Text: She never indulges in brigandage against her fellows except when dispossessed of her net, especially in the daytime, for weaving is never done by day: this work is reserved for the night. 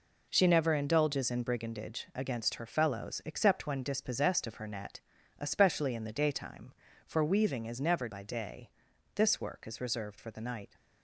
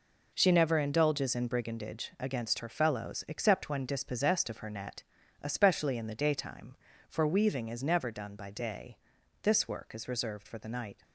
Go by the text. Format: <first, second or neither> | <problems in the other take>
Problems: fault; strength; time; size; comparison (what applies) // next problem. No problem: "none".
second | skips "done"; at 8.0 s